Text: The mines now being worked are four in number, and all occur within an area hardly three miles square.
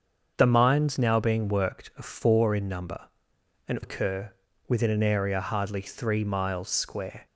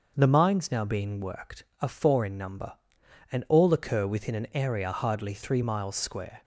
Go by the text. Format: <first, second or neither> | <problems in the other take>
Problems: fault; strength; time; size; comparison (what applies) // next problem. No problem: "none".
second | starts louder than the rest; until 1.3 s; 7 dB; also in the second // skips "all"; at 3.7 s // pauses between "occur" and "within"; slight; at 4.3 s; 0.36 s long